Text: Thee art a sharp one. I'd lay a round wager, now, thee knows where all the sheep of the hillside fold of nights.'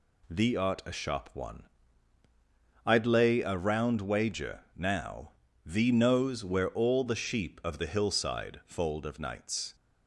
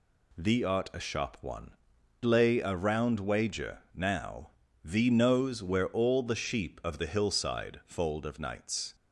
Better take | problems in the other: first | skips "I'd"; at 1.9 s

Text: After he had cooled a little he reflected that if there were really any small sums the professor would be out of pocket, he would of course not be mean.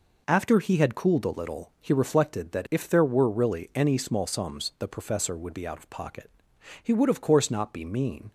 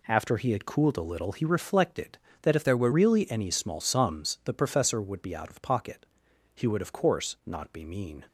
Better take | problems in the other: first | changes voice from "there" to "were"; from 2.6 to 2.8 s; 0.2 s long

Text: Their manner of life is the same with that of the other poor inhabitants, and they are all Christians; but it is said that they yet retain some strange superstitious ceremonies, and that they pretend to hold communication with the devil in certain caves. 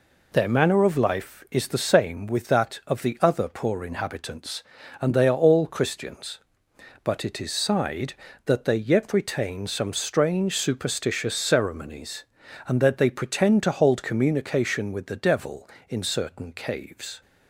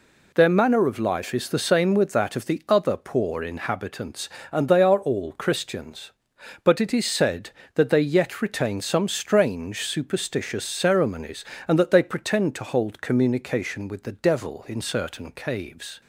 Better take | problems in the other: second | says "sighed" for "said"; at 7.5 s

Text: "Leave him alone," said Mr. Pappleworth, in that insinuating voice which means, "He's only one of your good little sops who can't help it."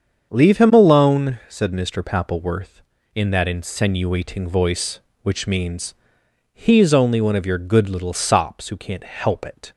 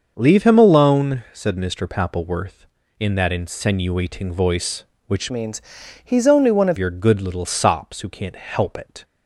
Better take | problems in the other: first | starts louder than the rest; until 1.1 s; 6.5 dB; also in the first // changes voice from "means" to "of"; from 5.3 to 6.7 s; 1.4 s long

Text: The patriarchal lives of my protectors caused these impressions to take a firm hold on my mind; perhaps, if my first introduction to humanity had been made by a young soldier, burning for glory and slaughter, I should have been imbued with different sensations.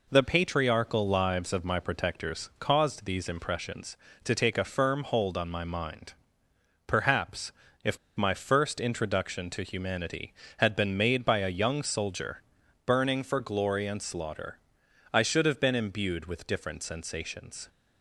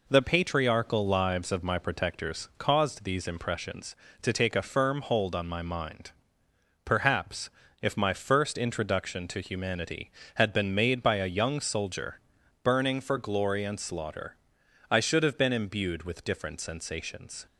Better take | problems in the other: second | pauses between "if" and "my"; slight; at 7.9 s; 0.20 s long

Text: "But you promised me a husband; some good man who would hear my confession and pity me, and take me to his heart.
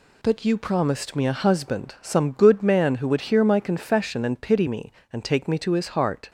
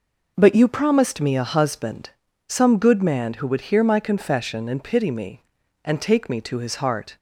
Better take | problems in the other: neither | none

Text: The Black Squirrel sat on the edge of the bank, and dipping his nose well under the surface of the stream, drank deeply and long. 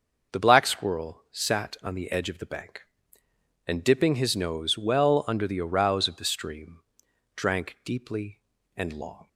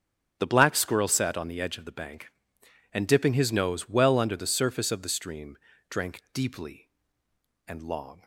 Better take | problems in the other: second | starts louder than the rest; noticeable; until 1.4 s; 6 dB; also in the second // says "arouse" for "surface"; at 5.6 s

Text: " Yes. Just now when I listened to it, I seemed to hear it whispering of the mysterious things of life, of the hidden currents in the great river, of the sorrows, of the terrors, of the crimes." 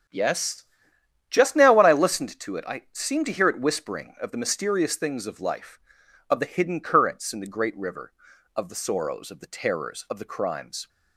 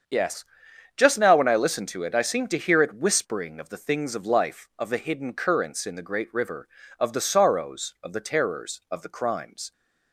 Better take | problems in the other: first | starts louder than the rest; strong; until 1.5 s; 7.5 dB; strong in the first // skips "mysterious"; at 3.7 s

